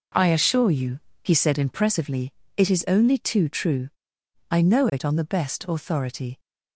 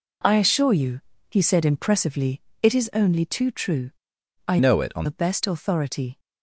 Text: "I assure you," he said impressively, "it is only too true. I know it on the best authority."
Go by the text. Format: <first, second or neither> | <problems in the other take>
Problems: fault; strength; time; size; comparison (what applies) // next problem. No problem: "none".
first | changes voice from "know" to "on"; from 4.5 to 5.0 s; 0.5 s long